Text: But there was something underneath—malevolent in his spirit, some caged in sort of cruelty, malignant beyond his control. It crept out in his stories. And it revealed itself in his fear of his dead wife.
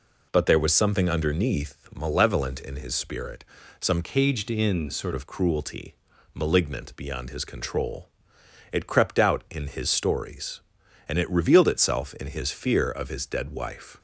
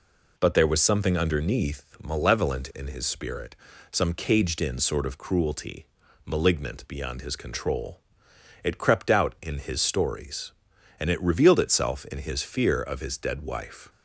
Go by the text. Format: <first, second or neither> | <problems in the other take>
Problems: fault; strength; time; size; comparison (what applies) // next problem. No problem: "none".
second | changes voice from "caged" to "sort"; from 4.0 to 5.1 s; 1.1 s long